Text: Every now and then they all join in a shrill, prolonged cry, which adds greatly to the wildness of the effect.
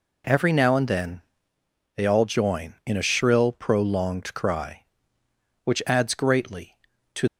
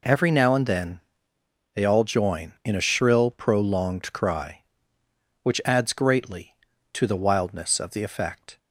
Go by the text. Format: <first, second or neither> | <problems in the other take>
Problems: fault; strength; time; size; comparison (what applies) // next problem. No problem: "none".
second | pauses between "then" and "they"; noticeable; at 1.2 s; 0.74 s long; noticeable in the second // stops before "the wildness of the effect"; at 7.2 s